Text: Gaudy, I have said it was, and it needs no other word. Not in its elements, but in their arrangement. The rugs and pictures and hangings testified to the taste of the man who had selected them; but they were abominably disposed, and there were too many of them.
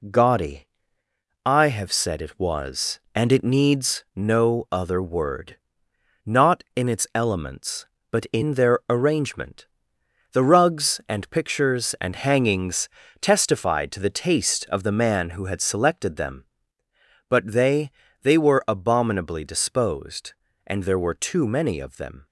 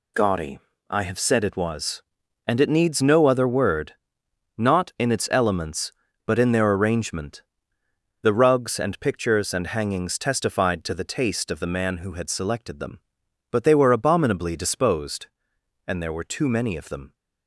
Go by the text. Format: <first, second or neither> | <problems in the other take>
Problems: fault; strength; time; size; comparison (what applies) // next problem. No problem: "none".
second | pauses between "hangings" and "testified"; slight; at 12.8 s; 0.32 s long // says "they" twice; at 18.2 s